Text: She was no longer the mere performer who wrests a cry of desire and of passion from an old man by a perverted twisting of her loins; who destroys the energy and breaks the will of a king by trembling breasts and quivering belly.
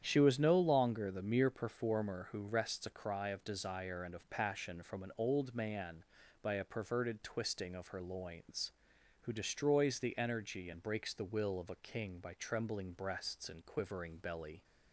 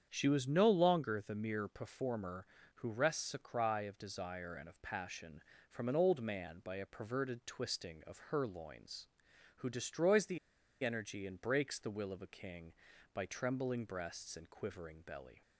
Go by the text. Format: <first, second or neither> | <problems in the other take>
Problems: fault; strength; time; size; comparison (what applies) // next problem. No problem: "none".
first | starts louder than the rest; strong; until 1.1 s; 8 dB; strong in the first // pauses between "the" and "energy"; at 10.3 s; 0.44 s long